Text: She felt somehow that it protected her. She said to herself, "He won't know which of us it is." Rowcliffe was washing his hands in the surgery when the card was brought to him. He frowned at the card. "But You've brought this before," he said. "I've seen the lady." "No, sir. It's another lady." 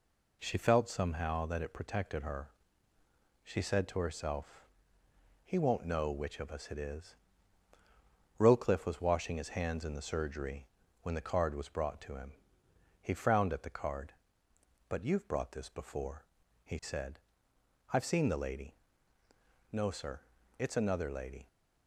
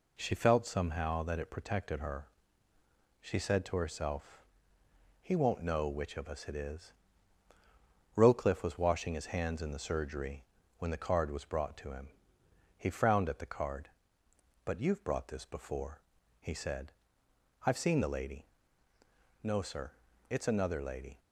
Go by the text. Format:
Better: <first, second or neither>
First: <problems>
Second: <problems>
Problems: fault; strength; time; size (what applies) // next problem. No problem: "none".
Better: neither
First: pauses between "surgery" and "when"; slight; at 10.6 s; 0.36 s long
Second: pauses between "surgery" and "when"; slight; at 10.4 s; 0.34 s long